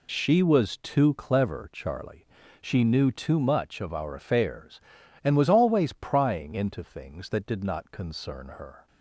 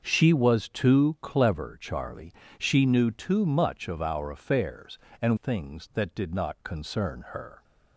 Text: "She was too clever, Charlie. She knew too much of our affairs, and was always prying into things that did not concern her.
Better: first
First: none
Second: starts louder than the rest; until 1.0 s; 6.5 dB // skips "was always prying into"; at 5.3 s

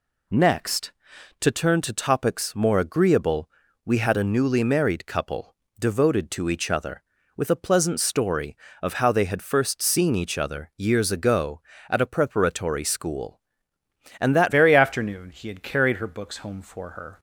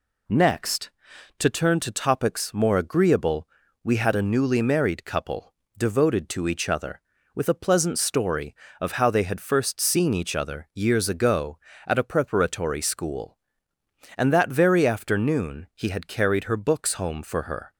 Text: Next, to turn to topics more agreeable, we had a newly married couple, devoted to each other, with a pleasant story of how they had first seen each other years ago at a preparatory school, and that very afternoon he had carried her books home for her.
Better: second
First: changes voice at "very"; from 14.5 s on; 2.6 s long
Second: none

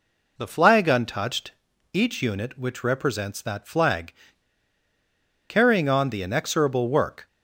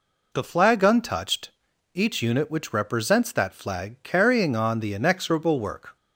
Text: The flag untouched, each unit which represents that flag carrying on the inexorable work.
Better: second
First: pauses between "flag" and "carrying"; strong; at 4.1 s; 1.3 s long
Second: none

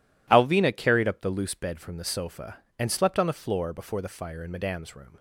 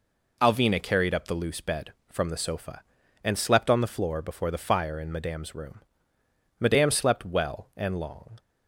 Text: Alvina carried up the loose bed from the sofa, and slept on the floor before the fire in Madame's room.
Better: first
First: none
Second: goes on to say "Madame slept well and long"; strong; from 6.6 s on; 1.7 s long

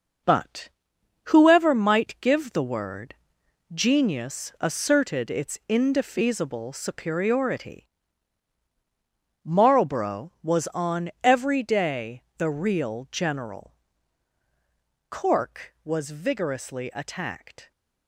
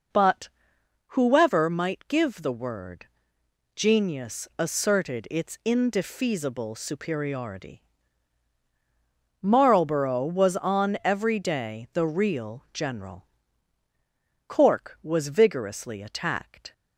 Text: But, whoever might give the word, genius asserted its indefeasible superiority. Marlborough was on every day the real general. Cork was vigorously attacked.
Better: second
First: gets quieter; strong; throughout; 8 dB // pauses between "day" and "the"; slight; at 12.2 s; 0.16 s long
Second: none

